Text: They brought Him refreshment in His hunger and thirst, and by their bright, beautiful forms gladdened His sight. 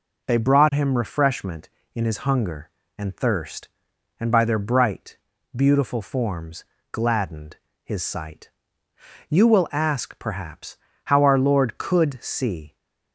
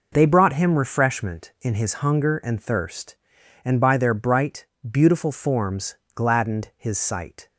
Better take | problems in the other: second | pauses between "forms" and "gladdened"; slight; at 6.6 s; 0.28 s long; slight in the second // pauses between "gladdened" and "His"; slight; at 7.5 s; 0.26 s long // goes on to say "You will ask perhaps how our Lord could see"; strong; from 9.2 s on; 3.4 s long

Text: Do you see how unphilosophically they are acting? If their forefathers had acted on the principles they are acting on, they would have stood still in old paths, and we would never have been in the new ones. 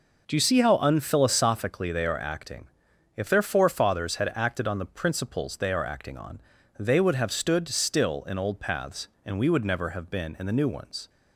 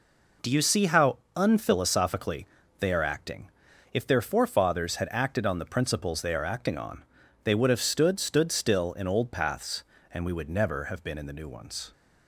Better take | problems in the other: first | pauses between "how" and "unphilosophically"; slight; at 1.1 s; 0.18 s long // pauses between "unphilosophically" and "they"; slight; at 2.4 s; 0.34 s long // says "stood" twice; at 8.1 s

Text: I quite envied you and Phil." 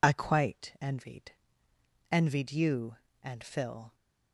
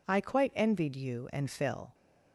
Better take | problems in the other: second | says "envied" twice; at 2.1 s

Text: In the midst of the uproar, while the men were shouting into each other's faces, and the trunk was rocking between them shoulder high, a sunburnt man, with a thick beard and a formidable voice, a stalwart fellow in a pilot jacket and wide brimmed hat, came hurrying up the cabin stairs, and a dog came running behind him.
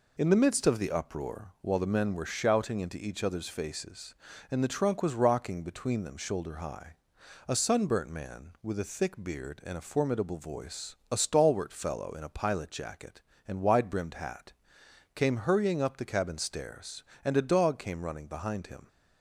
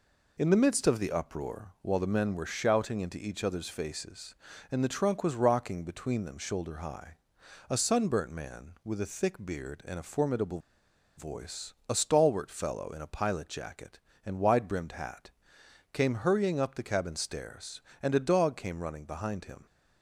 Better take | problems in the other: first | pauses between "formidable" and "voice"; noticeable; at 10.5 s; 0.58 s long

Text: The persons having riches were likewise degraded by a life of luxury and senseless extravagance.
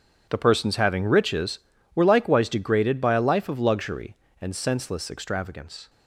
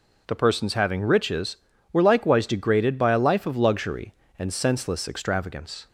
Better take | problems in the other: second | gets quieter; strong; throughout; 14 dB

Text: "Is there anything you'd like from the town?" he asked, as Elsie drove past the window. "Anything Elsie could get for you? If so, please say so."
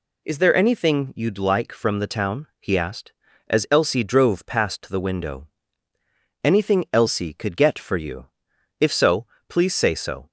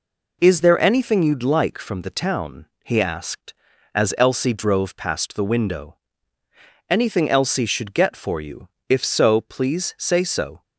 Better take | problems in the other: first | says "should" for "could"; at 7.6 s

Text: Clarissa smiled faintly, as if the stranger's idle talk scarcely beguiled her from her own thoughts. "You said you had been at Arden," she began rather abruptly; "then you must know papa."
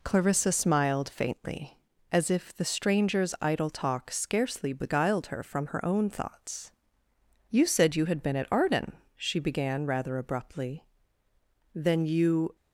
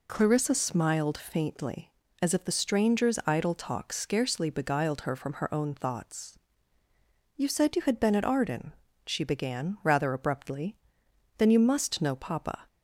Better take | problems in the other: second | stops before "must know papa"; at 12.5 s

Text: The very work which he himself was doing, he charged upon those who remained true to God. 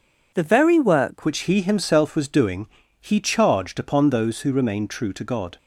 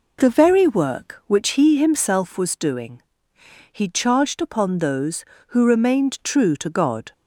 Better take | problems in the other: second | changes voice at "which"; from 1.2 s on; 4.3 s long

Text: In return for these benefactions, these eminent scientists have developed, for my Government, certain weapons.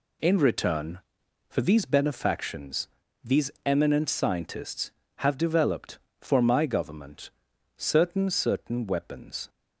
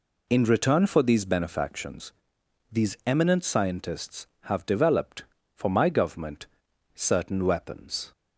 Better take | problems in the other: second | says "certain" twice; at 8.2 s

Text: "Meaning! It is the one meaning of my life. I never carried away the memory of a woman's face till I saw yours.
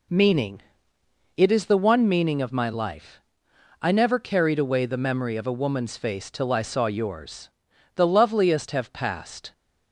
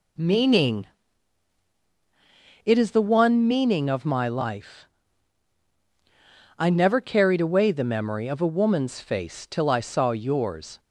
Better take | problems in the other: second | goes on to say "The loveliest have passed"; from 7.9 s on; 1.5 s long

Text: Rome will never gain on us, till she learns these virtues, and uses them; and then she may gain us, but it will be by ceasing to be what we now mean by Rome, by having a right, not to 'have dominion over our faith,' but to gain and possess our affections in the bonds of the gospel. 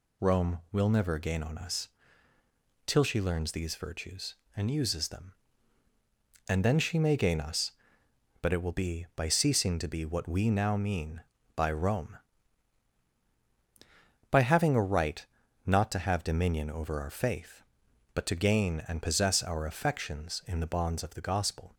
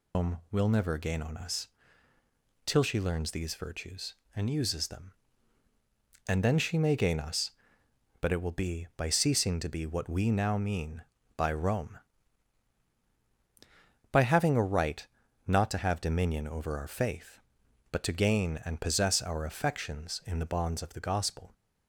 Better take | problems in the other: first | loses the start of "Rome"; at 0.1 s; 145 ms

